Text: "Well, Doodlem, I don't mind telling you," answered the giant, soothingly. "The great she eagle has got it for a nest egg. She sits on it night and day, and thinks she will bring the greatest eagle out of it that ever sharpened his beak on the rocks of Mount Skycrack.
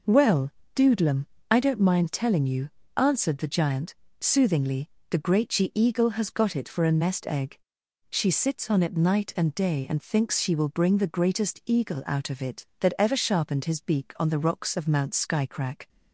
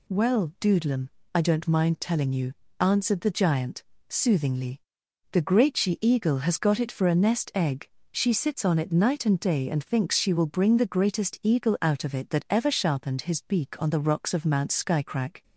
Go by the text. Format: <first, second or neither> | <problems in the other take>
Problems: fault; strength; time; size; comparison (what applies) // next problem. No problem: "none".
second | gets quieter; strong; throughout; 8 dB